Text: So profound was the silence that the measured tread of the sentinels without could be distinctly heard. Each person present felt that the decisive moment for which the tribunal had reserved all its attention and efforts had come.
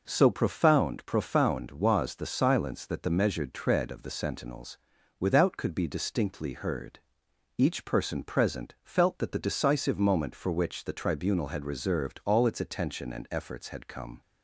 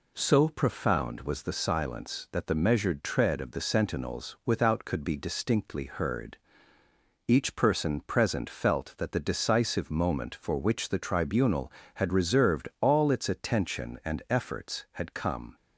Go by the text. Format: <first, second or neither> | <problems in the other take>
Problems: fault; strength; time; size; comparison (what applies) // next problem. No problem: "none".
second | says "profound" twice; at 1.0 s // pauses between "sentinels" and "without"; at 4.7 s; 0.40 s long